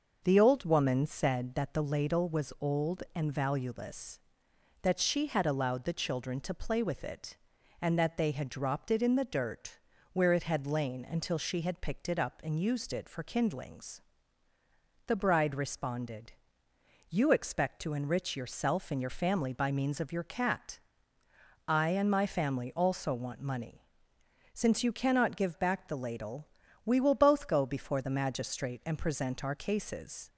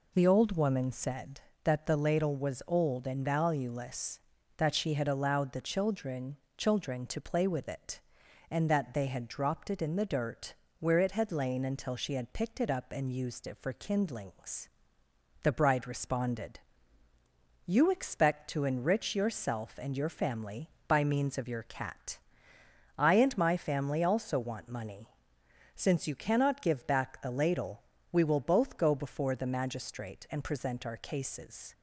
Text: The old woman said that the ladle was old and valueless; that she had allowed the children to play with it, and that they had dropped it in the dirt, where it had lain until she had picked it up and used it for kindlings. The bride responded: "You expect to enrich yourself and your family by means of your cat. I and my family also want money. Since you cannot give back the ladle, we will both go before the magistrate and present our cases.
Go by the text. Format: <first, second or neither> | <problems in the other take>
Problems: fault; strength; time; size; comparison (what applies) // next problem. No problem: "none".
first | says "children" twice; at 6.5 s